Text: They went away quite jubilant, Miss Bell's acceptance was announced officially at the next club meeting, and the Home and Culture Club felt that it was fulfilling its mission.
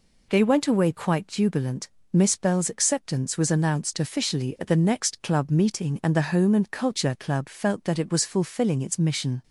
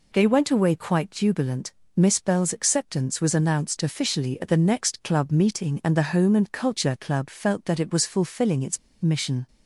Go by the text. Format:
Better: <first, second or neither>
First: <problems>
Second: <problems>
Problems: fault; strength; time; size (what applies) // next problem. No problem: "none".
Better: first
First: none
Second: pauses between "its" and "mission"; slight; at 8.7 s; 0.23 s long